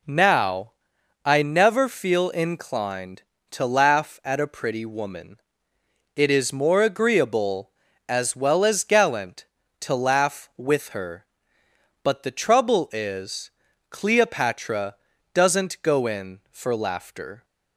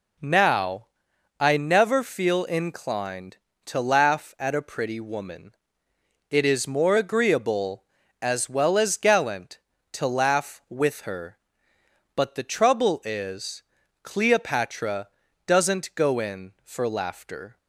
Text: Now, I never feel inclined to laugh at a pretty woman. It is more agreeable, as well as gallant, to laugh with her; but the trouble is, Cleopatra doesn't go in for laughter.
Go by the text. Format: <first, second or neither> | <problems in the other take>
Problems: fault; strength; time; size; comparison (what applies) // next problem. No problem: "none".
neither | pauses between "Cleopatra" and "doesn't"; the same in both